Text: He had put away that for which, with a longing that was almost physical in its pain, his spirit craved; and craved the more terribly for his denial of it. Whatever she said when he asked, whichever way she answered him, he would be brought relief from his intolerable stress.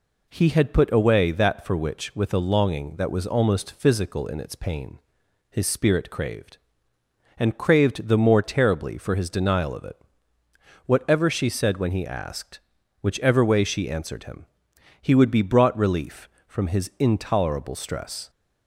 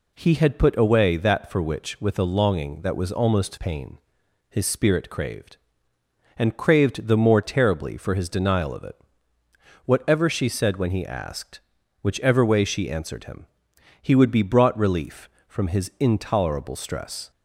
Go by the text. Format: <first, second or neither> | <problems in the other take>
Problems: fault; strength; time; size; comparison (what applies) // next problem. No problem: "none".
first | skips "physical in its"; at 3.5 s